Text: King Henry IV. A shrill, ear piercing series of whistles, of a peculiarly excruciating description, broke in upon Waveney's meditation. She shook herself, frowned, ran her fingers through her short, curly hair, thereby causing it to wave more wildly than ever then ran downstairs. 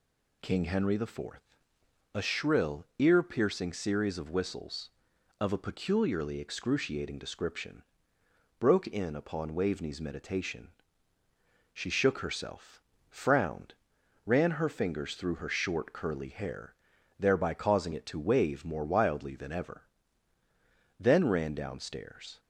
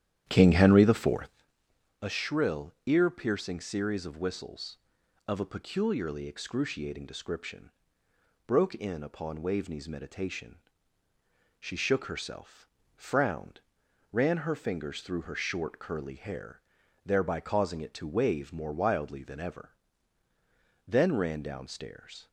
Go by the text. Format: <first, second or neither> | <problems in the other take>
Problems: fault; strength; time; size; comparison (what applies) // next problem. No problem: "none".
first | starts louder than the rest; strong; until 1.4 s; 11 dB // pauses between "ever" and "then"; at 19.6 s; 1.1 s long; also in the first